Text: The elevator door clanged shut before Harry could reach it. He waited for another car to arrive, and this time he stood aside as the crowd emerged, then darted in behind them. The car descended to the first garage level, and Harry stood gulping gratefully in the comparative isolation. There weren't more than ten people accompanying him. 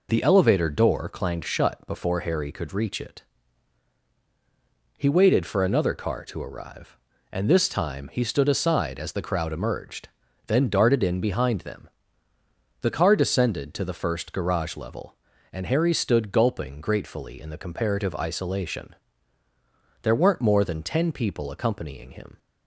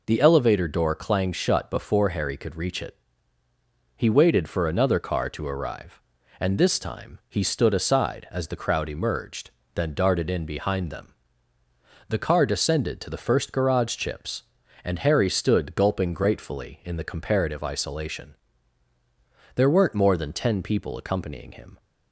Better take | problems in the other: first | says "chips" for "level"; at 13.9 s

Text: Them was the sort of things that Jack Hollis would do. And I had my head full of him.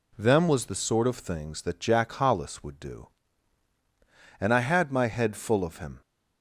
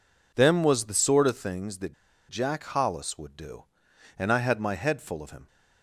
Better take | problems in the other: first | pauses between "that" and "Jack"; slight; at 1.9 s; 0.34 s long

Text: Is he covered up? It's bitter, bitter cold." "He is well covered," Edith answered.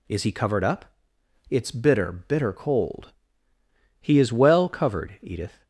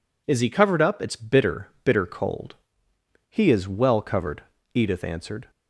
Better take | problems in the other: second | stops before "answered"; at 5.6 s

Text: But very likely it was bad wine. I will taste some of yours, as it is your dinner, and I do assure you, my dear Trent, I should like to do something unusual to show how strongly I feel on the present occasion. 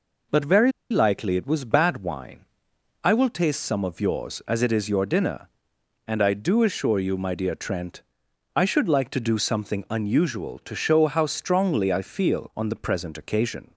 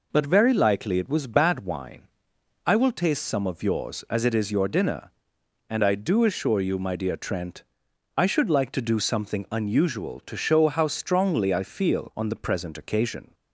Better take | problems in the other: second | pauses between "very" and "likely"; slight; at 0.7 s; 0.20 s long

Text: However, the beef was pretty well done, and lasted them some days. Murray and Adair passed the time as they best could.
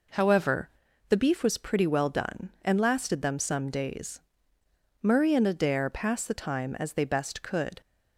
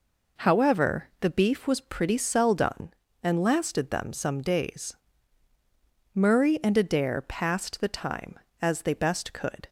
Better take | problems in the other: first | says "cell" for "well"; at 2.1 s

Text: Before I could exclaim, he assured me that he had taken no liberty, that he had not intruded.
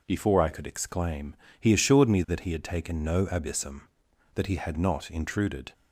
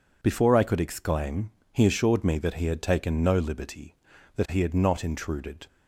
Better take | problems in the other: second | says "abyssum" for "liberty"; at 3.2 s

